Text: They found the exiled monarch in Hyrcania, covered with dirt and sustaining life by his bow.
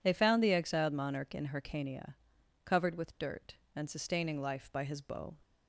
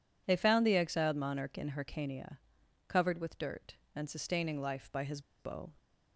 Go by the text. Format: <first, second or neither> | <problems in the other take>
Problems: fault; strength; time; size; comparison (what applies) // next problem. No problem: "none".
first | pauses between "his" and "bow"; slight; at 5.1 s; 0.19 s long